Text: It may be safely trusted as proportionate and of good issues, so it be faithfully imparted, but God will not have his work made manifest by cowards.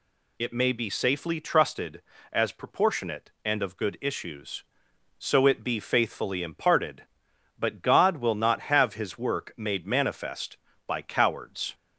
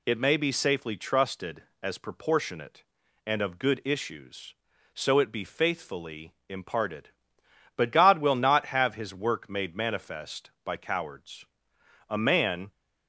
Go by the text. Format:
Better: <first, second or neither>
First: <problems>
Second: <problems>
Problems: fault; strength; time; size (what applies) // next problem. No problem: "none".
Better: first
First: none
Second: pauses between "faithfully" and "imparted"; slight; at 6.3 s; 0.16 s long // goes on to say "A man"; noticeable; from 12.0 s on; 0.62 s long